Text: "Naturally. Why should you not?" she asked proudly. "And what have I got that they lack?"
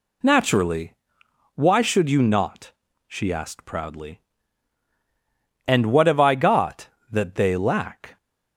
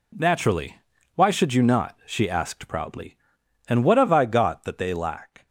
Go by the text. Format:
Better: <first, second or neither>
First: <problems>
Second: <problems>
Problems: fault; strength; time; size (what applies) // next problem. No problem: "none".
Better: neither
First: none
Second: none